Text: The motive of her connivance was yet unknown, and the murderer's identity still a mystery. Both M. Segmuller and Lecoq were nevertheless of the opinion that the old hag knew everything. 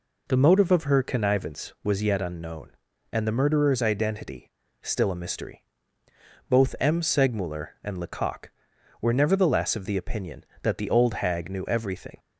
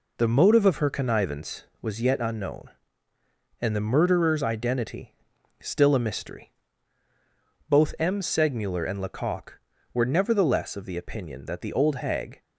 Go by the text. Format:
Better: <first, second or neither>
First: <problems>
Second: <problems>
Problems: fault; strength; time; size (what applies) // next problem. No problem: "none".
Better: first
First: pauses between "identity" and "still"; slight; at 4.5 s; 0.32 s long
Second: pauses between "identity" and "still"; at 5.1 s; 0.44 s long // stops before "knew everything"; at 12.4 s